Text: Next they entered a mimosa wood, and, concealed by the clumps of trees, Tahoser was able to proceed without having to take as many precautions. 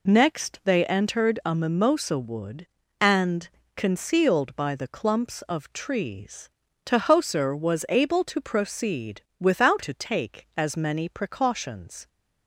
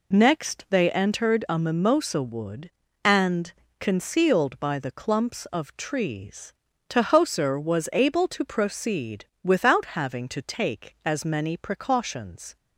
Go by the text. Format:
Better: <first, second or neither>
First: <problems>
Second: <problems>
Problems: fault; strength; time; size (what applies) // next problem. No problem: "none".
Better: second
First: pauses between "proceed" and "without"; slight; at 9.2 s; 0.18 s long // skips "having"; at 9.8 s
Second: pauses between "proceed" and "without"; slight; at 9.2 s; 0.18 s long